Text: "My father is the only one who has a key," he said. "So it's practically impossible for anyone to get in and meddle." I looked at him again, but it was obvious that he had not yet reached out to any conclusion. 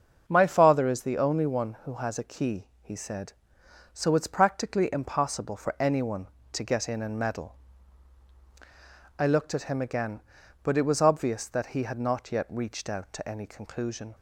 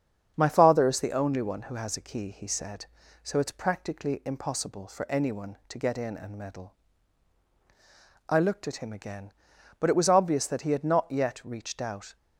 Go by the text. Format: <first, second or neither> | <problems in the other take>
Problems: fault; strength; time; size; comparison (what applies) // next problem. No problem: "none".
first | starts louder than the rest; strong; until 1.3 s; 8 dB; also in the first // stops before "to any conclusion"; at 12.1 s